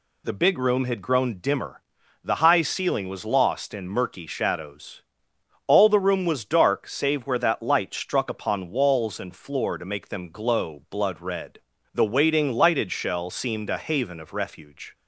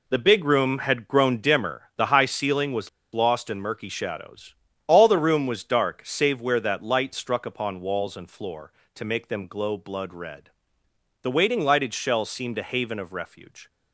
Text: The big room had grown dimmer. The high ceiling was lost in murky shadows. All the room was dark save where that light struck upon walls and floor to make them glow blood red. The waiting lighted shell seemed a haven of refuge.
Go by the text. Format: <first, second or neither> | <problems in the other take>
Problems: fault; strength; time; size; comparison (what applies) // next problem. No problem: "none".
first | pauses between "was" and "lost"; slight; at 2.8 s; 0.25 s long